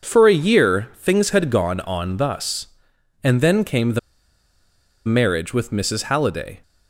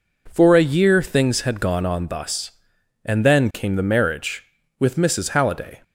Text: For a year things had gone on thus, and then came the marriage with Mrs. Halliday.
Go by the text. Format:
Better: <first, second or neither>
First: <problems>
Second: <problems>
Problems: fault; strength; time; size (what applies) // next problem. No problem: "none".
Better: second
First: pauses between "the" and "marriage"; at 3.9 s; 1.0 s long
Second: none